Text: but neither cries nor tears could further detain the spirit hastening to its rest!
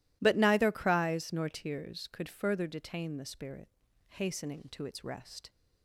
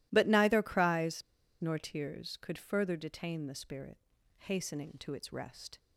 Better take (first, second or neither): first